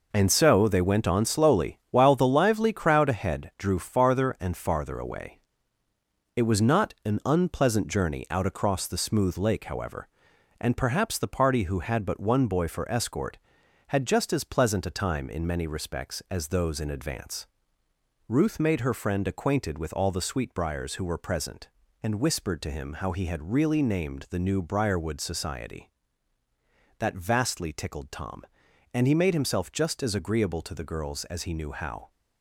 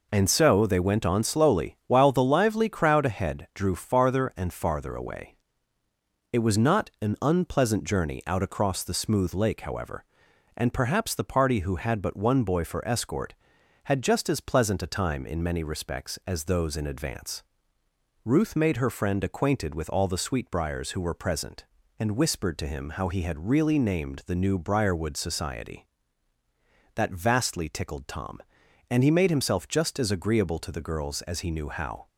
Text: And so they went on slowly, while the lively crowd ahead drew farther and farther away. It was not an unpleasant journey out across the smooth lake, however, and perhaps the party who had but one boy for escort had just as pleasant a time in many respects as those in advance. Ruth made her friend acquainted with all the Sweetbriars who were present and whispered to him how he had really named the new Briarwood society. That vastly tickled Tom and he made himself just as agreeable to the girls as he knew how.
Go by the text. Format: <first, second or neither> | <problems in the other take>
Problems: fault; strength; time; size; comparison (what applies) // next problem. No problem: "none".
second | gets quieter; strong; throughout; 7.5 dB